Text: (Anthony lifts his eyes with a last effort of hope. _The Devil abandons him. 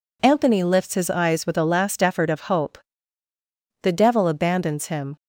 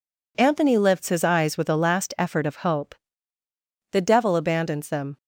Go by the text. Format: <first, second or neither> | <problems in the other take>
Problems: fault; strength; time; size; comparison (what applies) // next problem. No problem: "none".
first | says "them" for "him"; at 4.8 s